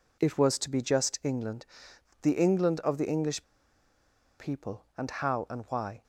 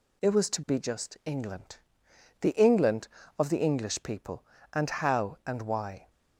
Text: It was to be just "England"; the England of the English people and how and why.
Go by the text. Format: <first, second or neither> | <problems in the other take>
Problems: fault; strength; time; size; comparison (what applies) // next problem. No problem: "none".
second | pauses between "English" and "people"; noticeable; at 3.4 s; 0.97 s long